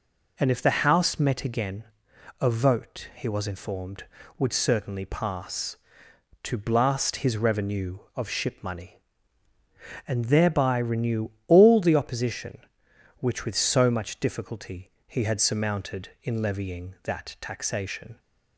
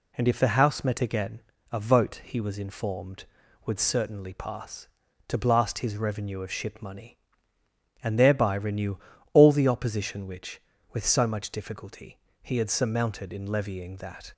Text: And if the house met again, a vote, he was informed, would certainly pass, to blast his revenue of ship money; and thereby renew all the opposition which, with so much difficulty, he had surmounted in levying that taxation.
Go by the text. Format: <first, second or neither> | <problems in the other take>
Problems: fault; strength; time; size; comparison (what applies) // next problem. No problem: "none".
first | pauses between "renew" and "all"; slight; at 8.9 s; 0.36 s long; slight in the first // stops before "taxation"; at 14.3 s